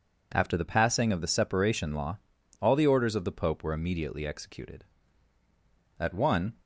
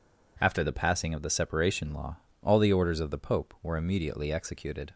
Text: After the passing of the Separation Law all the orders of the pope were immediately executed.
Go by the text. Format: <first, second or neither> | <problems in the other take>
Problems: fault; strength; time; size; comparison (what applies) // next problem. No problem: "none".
second | pauses between "Law" and "all"; at 2.1 s; 0.42 s long; slight in the second // goes on to say "At one"; from 5.9 s on; 0.56 s long